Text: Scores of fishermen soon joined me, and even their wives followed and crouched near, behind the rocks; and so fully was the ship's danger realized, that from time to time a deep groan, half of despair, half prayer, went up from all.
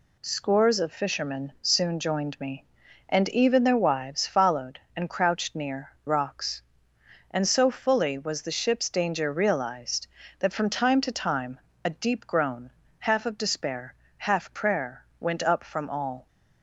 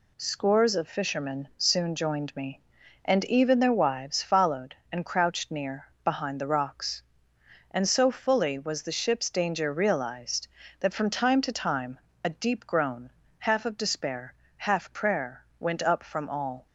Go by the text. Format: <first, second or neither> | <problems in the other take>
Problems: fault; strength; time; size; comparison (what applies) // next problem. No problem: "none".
second | skips "behind the"; at 5.9 s // pauses between "time" and "a"; slight; at 11.5 s; 0.26 s long; slight in the second